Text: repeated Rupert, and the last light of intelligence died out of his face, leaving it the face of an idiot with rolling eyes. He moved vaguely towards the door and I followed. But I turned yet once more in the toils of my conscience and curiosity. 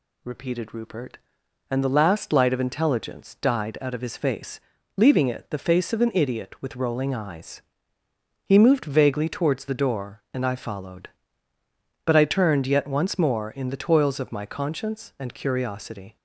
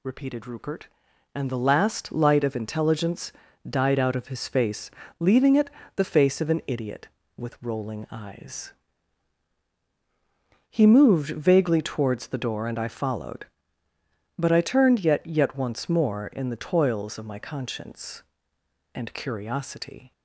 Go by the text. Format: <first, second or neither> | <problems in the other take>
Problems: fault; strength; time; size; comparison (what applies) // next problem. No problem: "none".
first | pauses between "intelligence" and "died"; slight; at 3.3 s; 0.36 s long // pauses between "it" and "the"; slight; at 5.6 s; 0.26 s long // says "yet" twice; at 15.2 s